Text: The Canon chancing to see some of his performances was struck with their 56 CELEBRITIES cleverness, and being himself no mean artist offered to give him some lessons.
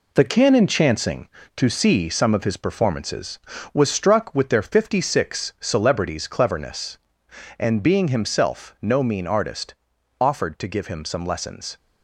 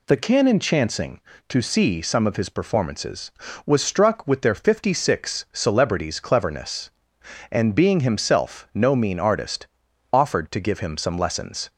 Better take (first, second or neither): second